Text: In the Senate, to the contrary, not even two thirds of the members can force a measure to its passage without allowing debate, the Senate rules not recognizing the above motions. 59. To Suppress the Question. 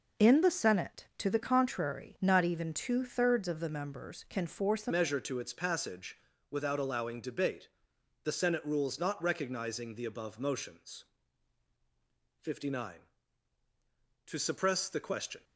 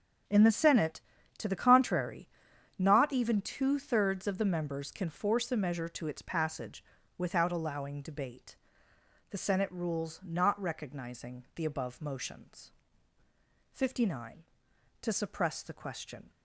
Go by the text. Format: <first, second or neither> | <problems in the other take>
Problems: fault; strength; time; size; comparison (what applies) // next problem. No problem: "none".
second | changes voice at "measure"; from 4.9 s on; 10.5 s long // pauses between "passage" and "without"; slight; at 6.1 s; 0.32 s long; slight in the second